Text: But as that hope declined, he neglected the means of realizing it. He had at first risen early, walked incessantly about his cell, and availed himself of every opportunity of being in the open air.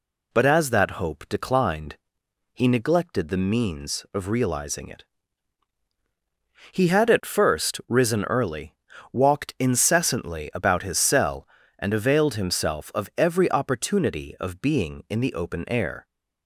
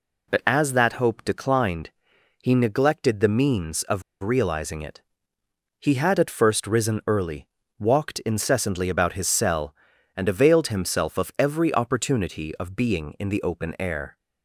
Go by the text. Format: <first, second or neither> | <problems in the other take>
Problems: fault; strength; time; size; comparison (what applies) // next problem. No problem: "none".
first | pauses between "of" and "realizing"; slight; at 4.0 s; 0.21 s long